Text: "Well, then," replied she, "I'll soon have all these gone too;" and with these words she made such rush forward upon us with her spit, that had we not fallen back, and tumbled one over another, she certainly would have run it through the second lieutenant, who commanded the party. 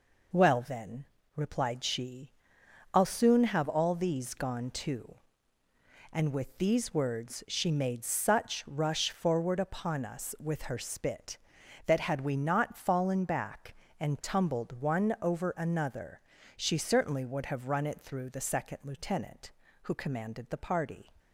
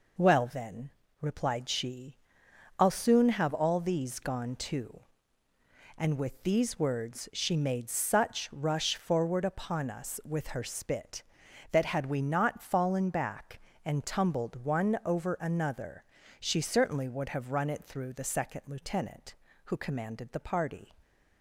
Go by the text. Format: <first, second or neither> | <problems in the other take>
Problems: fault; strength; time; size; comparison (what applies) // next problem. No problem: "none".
neither | none